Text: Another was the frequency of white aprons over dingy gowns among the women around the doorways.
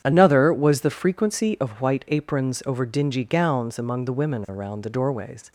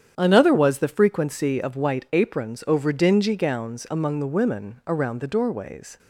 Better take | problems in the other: neither | starts louder than the rest; strong; the same in both

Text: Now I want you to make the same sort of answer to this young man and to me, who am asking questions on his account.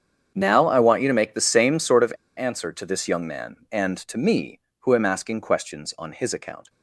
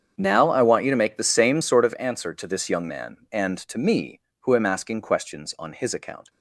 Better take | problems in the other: second | starts louder than the rest; strong; until 1.3 s; 7.5 dB; strong in the second // pauses between "of" and "answer"; slight; at 2.1 s; 0.26 s long

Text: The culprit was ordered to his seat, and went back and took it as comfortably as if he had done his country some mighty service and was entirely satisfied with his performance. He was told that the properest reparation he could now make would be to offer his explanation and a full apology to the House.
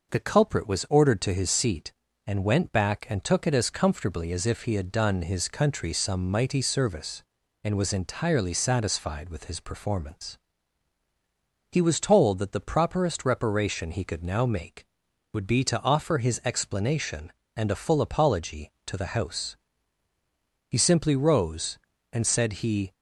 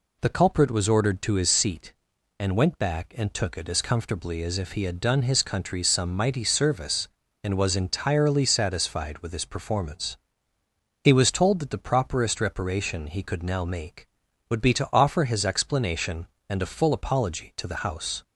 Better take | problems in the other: second | goes on to say "He simply rose and said he"; strong; from 20.6 s on; 2.2 s long

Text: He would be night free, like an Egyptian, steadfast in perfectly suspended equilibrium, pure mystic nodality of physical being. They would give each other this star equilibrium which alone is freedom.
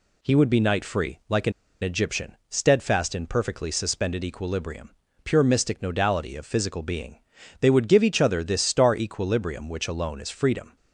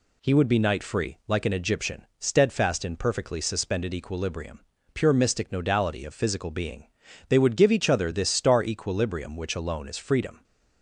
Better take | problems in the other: second | pauses between "an" and "Egyptian"; slight; at 1.5 s; 0.31 s long

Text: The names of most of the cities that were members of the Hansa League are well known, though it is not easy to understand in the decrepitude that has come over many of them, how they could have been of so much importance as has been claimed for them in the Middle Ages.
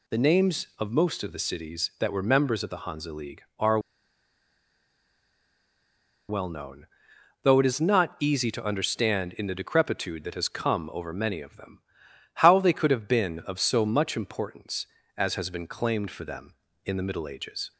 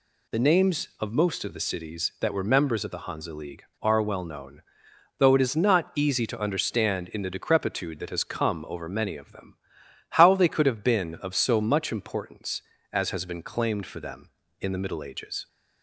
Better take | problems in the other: second | pauses between "are" and "well"; strong; at 3.7 s; 2.5 s long

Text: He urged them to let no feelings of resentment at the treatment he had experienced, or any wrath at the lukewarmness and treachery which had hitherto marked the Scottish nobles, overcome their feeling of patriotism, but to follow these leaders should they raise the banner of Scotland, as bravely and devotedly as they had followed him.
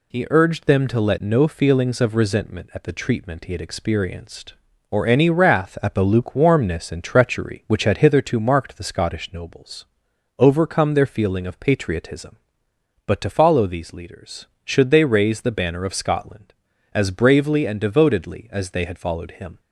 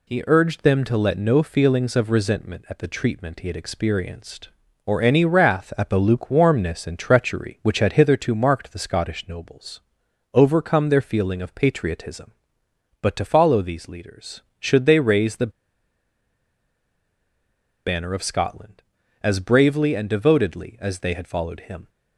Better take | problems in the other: first | pauses between "the" and "banner"; strong; at 15.5 s; 2.3 s long

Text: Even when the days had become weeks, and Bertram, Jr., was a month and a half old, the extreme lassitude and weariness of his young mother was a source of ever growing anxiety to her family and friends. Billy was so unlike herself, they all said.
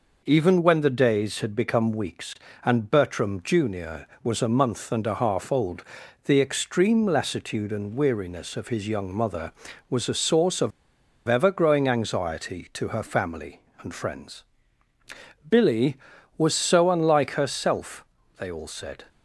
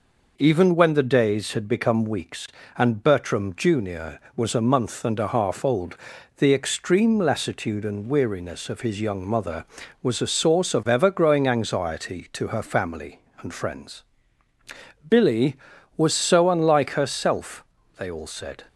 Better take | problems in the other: second | pauses between "of" and "ever"; noticeable; at 10.7 s; 0.57 s long

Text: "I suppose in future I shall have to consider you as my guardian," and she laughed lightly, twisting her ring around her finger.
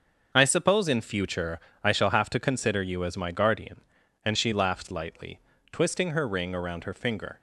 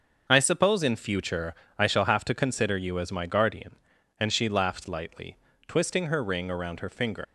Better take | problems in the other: first | starts louder than the rest; until 1.3 s; 6.5 dB; also in the first // pauses between "future" and "I"; slight; at 1.5 s; 0.24 s long; slight in the first // leaves "finger" unfinished; at 7.2 s; 100 ms

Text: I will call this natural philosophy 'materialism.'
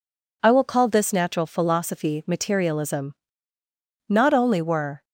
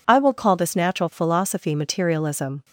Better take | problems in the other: second | goes on to say "Not only were"; noticeable; from 4.0 s on; 0.96 s long

